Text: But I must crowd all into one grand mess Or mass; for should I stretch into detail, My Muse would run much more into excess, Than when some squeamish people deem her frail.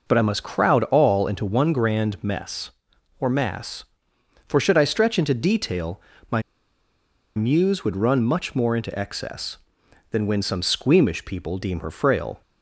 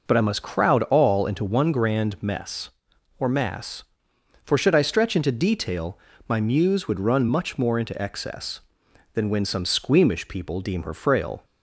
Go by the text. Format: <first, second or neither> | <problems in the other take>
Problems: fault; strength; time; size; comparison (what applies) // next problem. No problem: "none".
second | pauses between "My" and "Muse"; noticeable; at 6.4 s; 0.94 s long